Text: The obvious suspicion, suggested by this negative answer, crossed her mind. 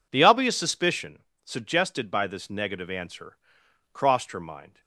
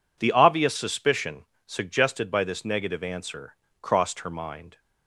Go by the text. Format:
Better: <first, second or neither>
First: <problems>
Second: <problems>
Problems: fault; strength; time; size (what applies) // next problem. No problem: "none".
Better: neither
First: none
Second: none